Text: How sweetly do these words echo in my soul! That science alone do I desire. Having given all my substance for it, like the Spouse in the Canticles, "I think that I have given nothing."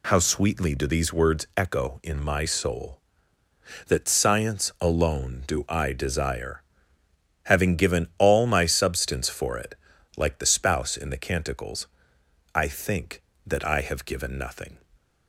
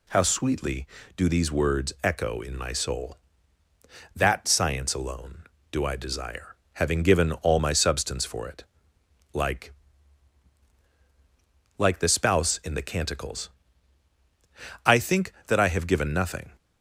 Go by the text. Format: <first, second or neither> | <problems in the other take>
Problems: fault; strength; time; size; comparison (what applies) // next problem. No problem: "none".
first | says "like" twice; at 11.7 s